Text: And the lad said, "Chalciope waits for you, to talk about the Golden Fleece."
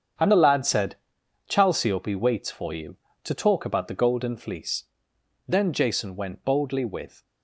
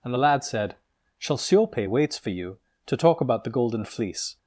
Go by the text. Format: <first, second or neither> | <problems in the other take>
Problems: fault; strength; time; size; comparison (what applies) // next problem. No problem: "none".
second | starts louder than the rest; strong; until 1.7 s; 7.5 dB // goes on to say "Then Jason went boldly with"; strong; from 5.4 s on; 1.7 s long